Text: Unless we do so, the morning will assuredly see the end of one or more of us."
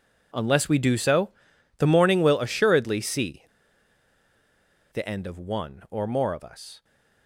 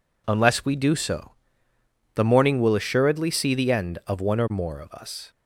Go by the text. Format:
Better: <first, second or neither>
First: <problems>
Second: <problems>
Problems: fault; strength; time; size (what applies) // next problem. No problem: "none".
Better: second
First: pauses between "see" and "the"; strong; at 3.4 s; 1.5 s long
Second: none